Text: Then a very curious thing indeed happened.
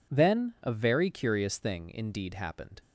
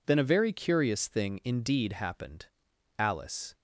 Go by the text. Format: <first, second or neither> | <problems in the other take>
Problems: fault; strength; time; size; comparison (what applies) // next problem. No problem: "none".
first | goes on to say "Alice"; from 2.9 s on; 0.58 s long